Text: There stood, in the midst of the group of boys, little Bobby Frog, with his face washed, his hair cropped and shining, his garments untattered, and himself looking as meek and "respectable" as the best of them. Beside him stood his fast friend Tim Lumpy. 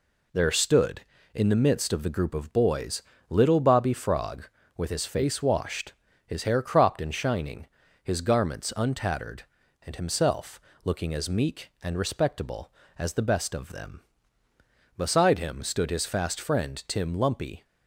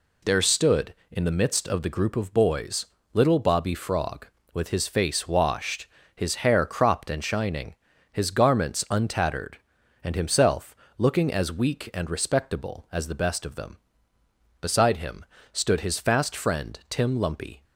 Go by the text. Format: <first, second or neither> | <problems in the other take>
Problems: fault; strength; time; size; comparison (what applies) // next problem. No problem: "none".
first | pauses between "himself" and "looking"; slight; at 10.7 s; 0.22 s long; slight in the first // says "weak" for "meek"; at 11.5 s // pauses between "him" and "stood"; slight; at 15.2 s; 0.26 s long